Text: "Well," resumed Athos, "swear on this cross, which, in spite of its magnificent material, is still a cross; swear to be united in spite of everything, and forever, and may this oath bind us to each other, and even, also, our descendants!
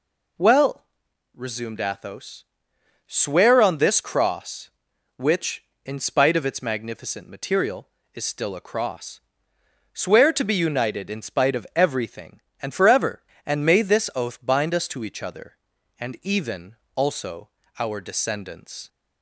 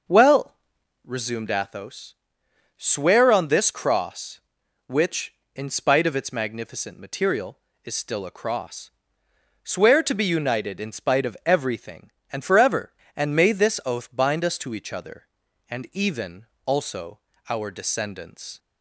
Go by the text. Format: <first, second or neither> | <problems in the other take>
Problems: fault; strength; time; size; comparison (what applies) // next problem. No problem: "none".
first | starts louder than the rest; noticeable; until 1.7 s; 6 dB